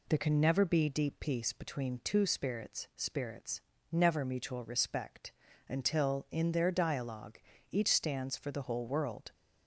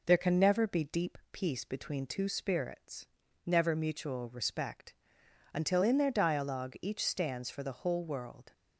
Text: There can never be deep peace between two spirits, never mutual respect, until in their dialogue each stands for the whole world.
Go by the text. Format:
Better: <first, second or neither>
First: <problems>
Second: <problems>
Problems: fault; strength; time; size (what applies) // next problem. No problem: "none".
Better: second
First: says "spirits" twice; at 2.9 s // pauses between "dialogue" and "each"; slight; at 7.3 s; 0.32 s long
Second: none